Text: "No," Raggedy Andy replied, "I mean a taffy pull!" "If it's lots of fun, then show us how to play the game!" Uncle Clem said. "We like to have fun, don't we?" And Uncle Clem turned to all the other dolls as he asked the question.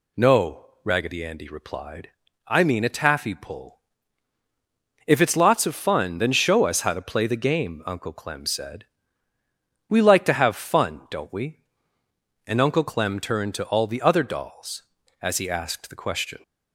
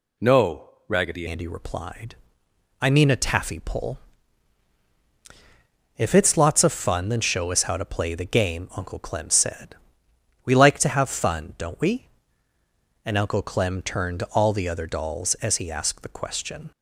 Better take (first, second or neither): first